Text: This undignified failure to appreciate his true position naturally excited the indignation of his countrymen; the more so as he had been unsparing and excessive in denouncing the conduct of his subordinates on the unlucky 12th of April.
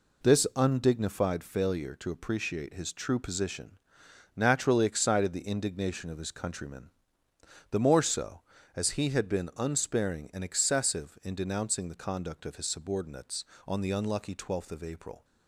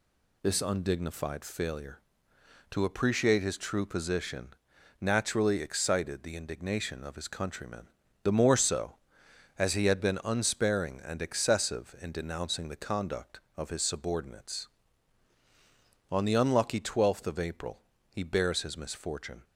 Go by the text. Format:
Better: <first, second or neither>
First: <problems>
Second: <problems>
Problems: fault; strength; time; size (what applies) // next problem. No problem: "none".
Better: first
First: pauses between "position" and "naturally"; noticeable; at 3.7 s; 0.58 s long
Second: pauses between "position" and "naturally"; noticeable; at 4.4 s; 0.50 s long // goes on to say "He bears his misfortune"; from 18.0 s on; 1.3 s long